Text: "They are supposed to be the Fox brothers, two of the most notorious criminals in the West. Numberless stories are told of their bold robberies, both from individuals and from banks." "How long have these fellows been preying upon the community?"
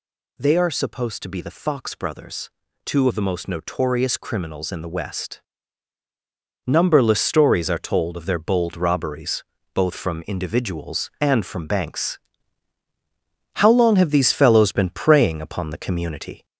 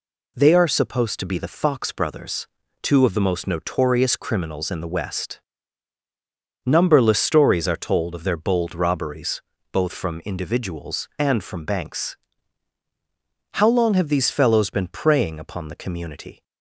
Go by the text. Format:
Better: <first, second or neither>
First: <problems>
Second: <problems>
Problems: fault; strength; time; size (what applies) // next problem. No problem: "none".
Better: second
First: gets louder; throughout; 3.5 dB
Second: none